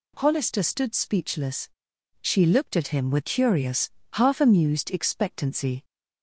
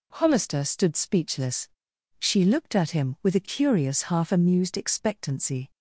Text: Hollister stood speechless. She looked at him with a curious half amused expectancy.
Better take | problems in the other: second | skips "a"; at 3.2 s // pauses between "curious" and "half"; slight; at 3.8 s; 0.24 s long

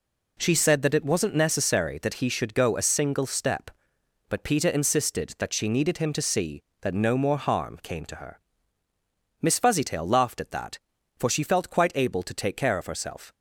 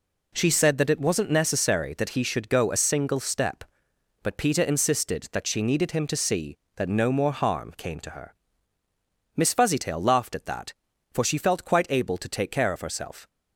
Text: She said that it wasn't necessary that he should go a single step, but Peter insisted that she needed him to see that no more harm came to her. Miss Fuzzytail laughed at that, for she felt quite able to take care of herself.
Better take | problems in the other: neither | none

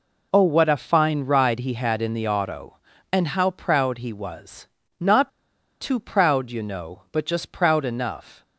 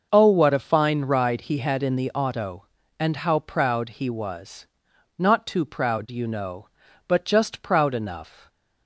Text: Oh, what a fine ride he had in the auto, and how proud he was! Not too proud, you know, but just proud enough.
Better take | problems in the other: second | pauses between "Not" and "too"; noticeable; at 5.2 s; 0.52 s long

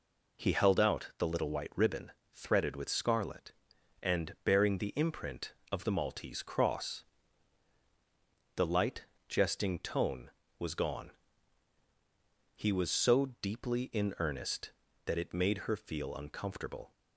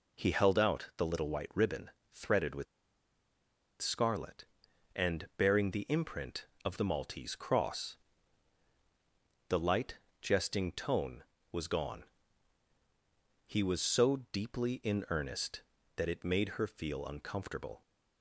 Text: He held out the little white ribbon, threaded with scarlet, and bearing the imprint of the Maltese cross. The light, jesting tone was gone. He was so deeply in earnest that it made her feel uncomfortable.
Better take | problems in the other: first | pauses between "with" and "scarlet"; at 2.6 s; 1.1 s long

